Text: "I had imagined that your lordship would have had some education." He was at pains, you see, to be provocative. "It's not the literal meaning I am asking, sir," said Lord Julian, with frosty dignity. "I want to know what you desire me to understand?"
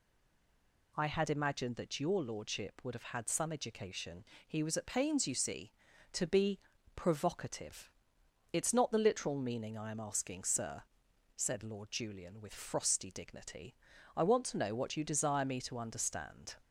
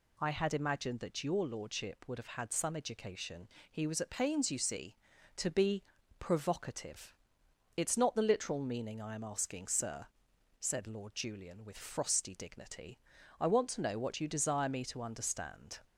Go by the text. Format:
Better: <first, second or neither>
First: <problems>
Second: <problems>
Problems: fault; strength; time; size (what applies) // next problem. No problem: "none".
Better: second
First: stays silent before the first word; slight; until 0.9 s; 0.9 s long // pauses between "be" and "provocative"; slight; at 6.5 s; 0.36 s long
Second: pauses between "be" and "provocative"; slight; at 5.8 s; 0.36 s long